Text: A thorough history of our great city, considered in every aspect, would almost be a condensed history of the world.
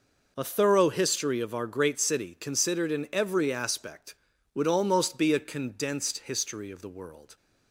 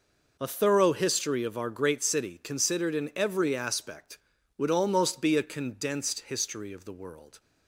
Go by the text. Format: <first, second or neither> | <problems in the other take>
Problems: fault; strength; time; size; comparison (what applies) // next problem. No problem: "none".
neither | none